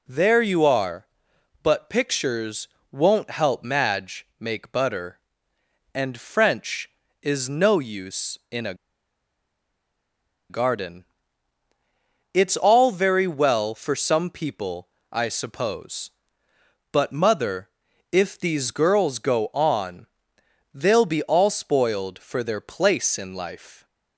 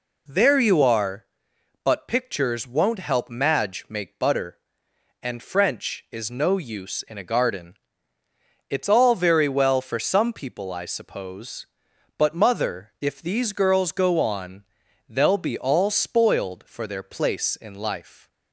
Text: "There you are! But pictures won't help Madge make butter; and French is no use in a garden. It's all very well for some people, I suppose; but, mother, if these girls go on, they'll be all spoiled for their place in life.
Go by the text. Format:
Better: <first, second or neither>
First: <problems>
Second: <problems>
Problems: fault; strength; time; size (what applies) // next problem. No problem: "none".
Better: second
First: pauses between "pictures" and "won't"; slight; at 2.6 s; 0.24 s long // pauses between "a" and "garden"; strong; at 8.7 s; 1.7 s long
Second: none